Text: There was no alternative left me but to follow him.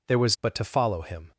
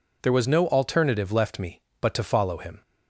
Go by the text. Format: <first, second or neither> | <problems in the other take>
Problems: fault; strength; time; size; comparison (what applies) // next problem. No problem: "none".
second | skips "no alternative left me"; at 0.3 s